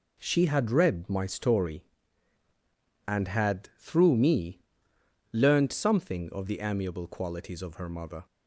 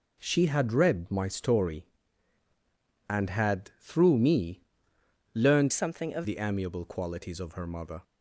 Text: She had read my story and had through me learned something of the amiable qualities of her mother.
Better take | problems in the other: first | pauses between "me" and "learned"; noticeable; at 4.6 s; 0.72 s long; noticeable in the first // changes voice from "something" to "of"; from 5.7 to 6.2 s; 0.5 s long

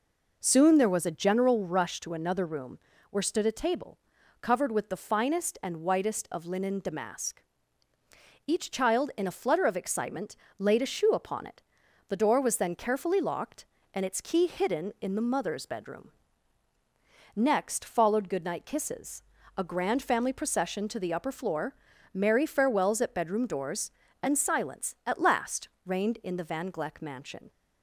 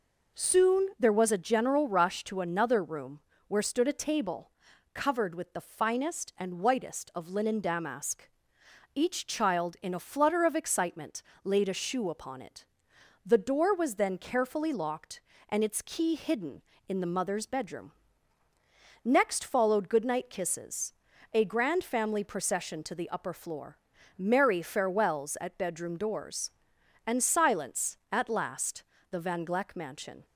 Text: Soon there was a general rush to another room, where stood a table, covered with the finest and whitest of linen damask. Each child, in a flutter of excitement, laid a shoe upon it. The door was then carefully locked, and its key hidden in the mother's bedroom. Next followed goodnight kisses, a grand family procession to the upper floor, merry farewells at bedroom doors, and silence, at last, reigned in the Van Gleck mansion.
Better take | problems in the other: first | skips "reigned in"; at 28.9 s

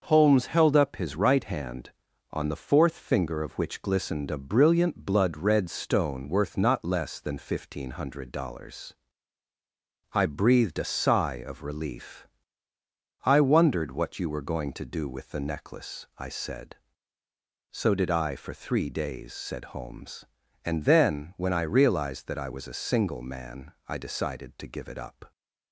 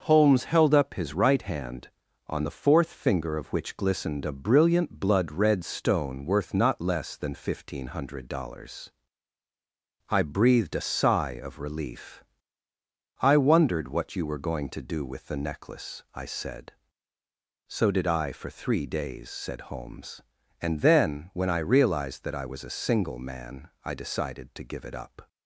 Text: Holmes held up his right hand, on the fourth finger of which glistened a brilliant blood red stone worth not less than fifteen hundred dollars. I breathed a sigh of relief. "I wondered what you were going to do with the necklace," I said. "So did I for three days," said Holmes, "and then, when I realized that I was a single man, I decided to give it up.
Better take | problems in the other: neither | starts louder than the rest; noticeable; the same in both

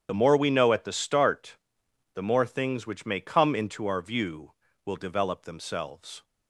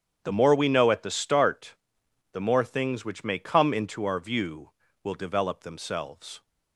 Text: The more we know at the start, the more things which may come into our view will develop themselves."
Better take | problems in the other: second | loses the start of "The"; at 0.0 s; 30 ms // starts louder than the rest; strong; until 1.1 s; 8.5 dB; strong in the second

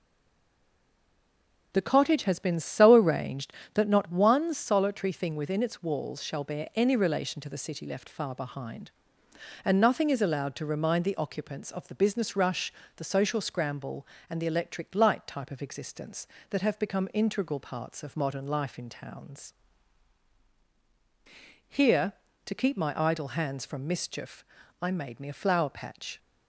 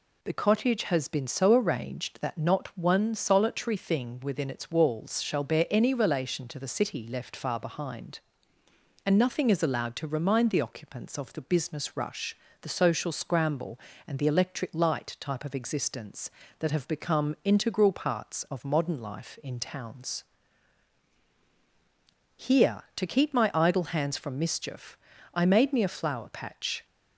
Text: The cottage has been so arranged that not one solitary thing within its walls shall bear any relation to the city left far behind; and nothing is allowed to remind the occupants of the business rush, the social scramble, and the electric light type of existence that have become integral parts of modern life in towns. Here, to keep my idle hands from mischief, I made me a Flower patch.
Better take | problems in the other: second | stays silent before the first word; noticeable; until 1.7 s; 1.7 s long

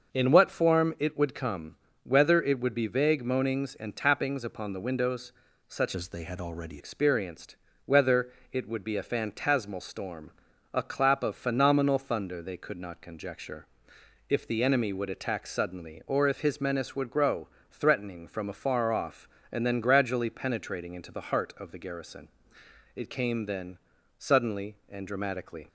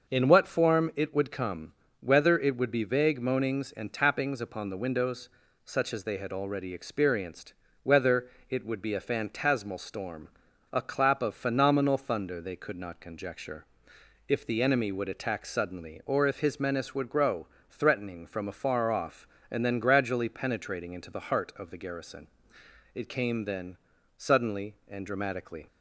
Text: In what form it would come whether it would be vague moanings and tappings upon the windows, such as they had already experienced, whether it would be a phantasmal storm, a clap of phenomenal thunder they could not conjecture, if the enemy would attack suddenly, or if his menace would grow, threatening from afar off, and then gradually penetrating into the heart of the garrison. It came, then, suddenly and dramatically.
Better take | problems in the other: second | starts louder than the rest; until 1.1 s; 6 dB; noticeable in the second // pauses between "come" and "whether"; slight; at 1.7 s; 0.26 s long; slight in the second // changes voice from "as" to "already"; from 5.9 to 6.8 s; 0.9 s long // pauses between "whether" and "it"; slight; at 8.3 s; 0.22 s long; slight in the second

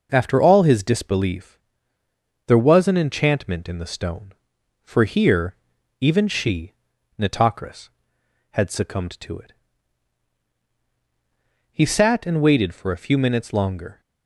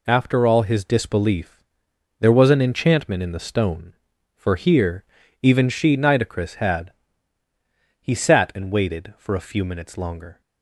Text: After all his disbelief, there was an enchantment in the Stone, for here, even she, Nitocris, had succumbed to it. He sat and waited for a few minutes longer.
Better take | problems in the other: first | skips "succumbed to it"; at 7.4 s

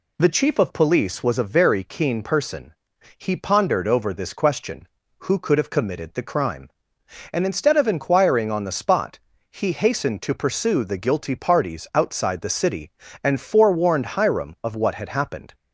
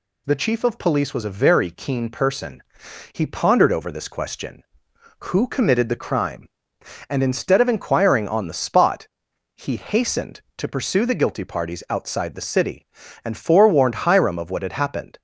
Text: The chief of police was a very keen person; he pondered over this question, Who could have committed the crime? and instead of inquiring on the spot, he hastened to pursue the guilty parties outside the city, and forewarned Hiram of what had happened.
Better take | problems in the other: first | skips "could have"; at 5.4 s

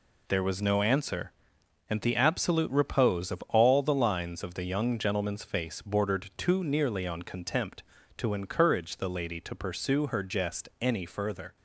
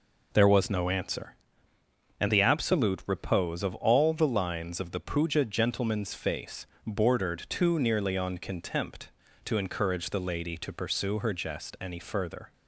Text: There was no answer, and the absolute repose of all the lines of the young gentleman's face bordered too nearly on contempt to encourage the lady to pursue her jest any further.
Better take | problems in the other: first | says "puja" for "young"; at 5.0 s // pauses between "face" and "bordered"; slight; at 6.6 s; 0.22 s long

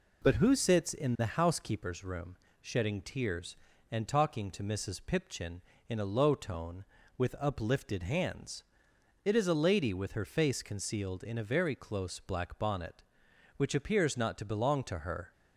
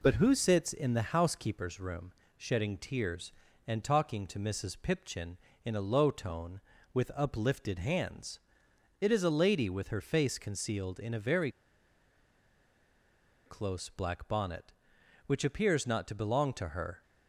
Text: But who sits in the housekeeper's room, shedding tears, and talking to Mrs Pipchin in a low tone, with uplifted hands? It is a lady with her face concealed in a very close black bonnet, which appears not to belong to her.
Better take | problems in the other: first | pauses between "very" and "close"; strong; at 11.5 s; 1.9 s long

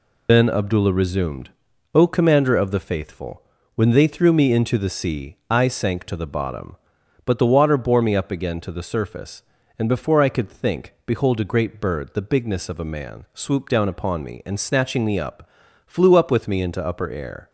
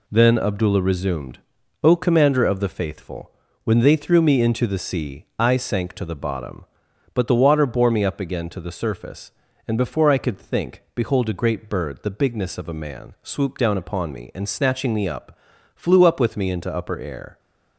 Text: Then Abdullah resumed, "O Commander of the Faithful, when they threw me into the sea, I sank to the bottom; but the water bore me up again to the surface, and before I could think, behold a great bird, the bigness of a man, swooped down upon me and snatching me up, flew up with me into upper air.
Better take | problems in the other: second | loses the start of "Then"; at 0.2 s; 100 ms

